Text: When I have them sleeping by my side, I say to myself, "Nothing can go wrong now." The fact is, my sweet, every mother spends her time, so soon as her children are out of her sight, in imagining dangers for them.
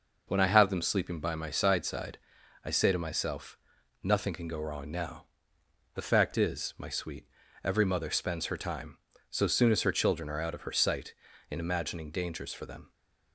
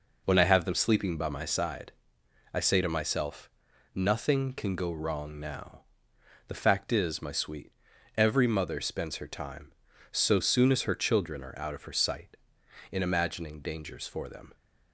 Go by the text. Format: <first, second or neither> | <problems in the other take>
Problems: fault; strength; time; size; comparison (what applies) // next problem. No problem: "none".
second | says "side" twice; at 1.8 s